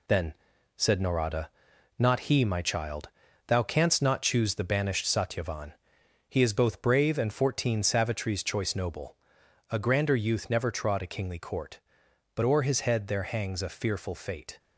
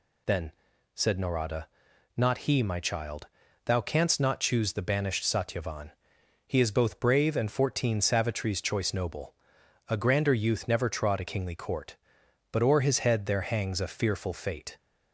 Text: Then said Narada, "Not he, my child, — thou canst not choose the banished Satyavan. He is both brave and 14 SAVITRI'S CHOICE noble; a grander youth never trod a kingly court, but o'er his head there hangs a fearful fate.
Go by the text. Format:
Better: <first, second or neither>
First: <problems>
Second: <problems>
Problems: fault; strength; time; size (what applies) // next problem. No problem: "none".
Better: second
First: gets quieter; noticeable; throughout; 5.5 dB // pauses between "Then" and "said"; at 0.3 s; 0.42 s long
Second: pauses between "Then" and "said"; at 0.5 s; 0.42 s long